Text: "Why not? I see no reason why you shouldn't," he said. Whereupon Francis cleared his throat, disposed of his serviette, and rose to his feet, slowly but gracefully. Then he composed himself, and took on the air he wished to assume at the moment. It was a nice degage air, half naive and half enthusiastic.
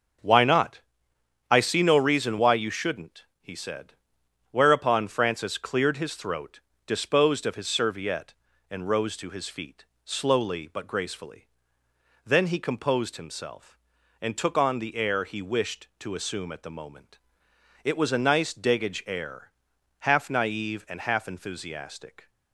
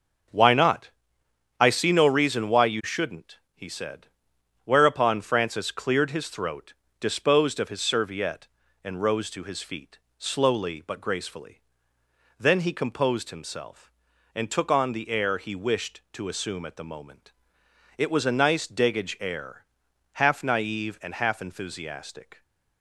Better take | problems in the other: neither | starts louder than the rest; the same in both

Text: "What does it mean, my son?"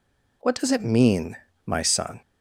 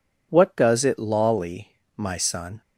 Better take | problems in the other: first | says "lolly" for "mean"; at 0.9 s

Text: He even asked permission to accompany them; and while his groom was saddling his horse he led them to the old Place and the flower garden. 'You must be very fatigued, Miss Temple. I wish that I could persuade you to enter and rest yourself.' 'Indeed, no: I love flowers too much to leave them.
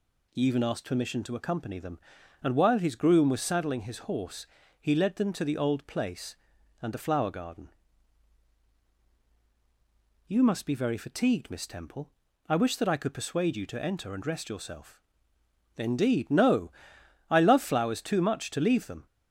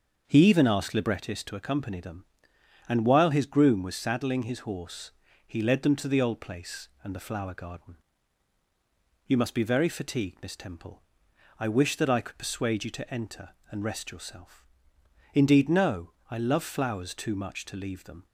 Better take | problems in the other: first | starts louder than the rest; until 1.2 s; 6.5 dB // says "librettist" for "permission"; at 0.9 s // pauses between "horse" and "he"; slight; at 5.1 s; 0.36 s long; slight in the first

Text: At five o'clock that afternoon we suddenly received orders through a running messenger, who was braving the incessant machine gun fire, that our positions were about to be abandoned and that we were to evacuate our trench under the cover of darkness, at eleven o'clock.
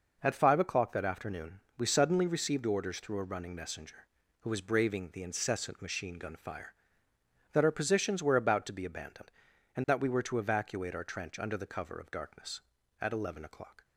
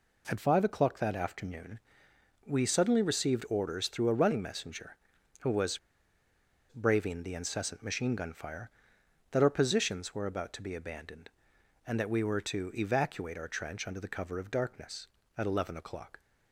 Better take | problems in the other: first | pauses between "afternoon" and "we"; noticeable; at 1.7 s; 0.70 s long; slight in the first // pauses between "was" and "braving"; noticeable; at 5.7 s; 0.91 s long

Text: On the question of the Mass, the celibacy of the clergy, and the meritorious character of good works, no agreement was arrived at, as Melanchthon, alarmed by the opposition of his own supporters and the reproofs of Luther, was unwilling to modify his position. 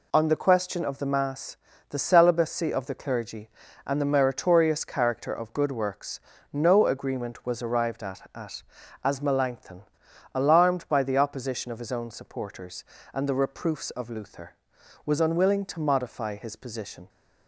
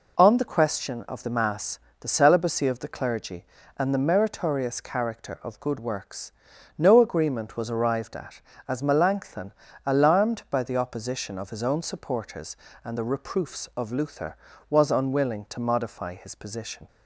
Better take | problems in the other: second | says "at" twice; at 8.3 s

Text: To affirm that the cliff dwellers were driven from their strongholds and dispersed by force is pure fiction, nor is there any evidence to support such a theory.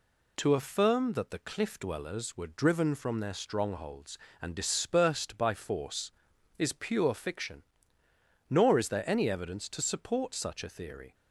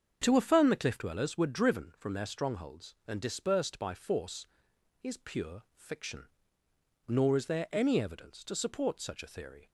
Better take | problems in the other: first | starts louder than the rest; until 1.2 s; 7 dB // skips "that"; at 0.6 s

